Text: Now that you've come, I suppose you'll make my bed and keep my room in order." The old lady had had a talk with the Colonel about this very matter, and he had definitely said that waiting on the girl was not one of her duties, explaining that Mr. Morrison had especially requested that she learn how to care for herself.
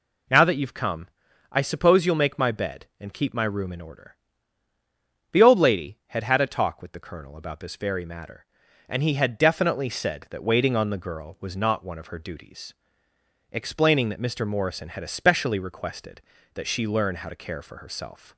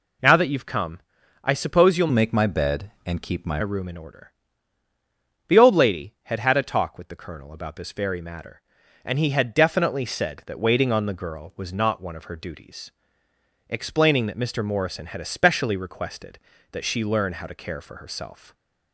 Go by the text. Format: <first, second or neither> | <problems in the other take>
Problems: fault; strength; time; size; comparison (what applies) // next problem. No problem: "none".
first | changes voice from "make" to "my"; from 2.1 to 3.5 s; 1.4 s long // stays silent after the last word; slight; from 18.3 s on; 0.6 s long